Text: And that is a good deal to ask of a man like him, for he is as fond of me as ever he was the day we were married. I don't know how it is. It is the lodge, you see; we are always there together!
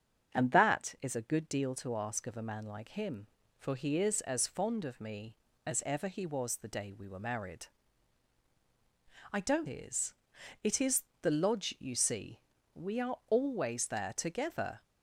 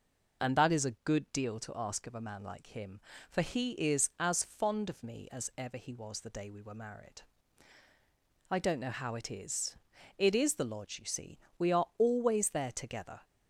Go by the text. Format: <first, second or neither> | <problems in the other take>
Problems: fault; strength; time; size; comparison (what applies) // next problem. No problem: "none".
second | starts louder than the rest; strong; until 1.3 s; 7.5 dB // skips "know how it"; at 9.6 s // pauses between "is" and "the"; slight; at 11.0 s; 0.18 s long